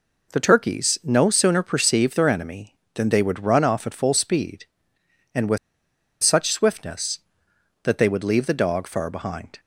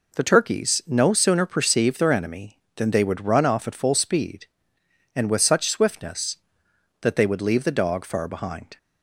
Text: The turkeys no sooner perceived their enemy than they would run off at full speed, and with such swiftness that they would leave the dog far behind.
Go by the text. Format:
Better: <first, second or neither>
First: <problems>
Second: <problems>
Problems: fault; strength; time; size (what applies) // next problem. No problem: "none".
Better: second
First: pauses between "with" and "such"; noticeable; at 5.5 s; 0.65 s long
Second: none